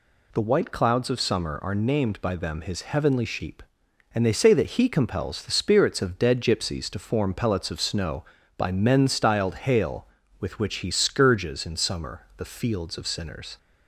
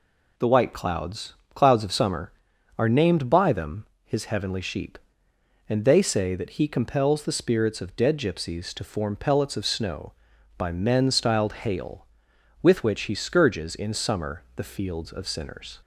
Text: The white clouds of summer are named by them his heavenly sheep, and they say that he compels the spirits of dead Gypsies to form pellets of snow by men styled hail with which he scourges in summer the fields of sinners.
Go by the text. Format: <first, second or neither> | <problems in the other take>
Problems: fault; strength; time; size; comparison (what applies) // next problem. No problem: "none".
first | says "clouds" twice; at 1.5 s // pauses between "them" and "his"; slight; at 3.8 s; 0.18 s long